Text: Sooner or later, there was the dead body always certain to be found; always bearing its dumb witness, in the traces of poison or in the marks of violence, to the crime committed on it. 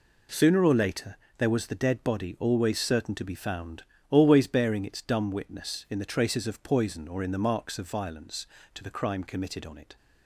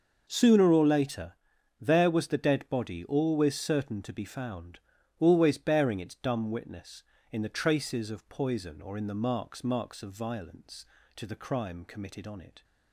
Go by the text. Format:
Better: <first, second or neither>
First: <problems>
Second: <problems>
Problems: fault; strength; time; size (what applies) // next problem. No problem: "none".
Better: first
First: none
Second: says "marks" twice; at 9.6 s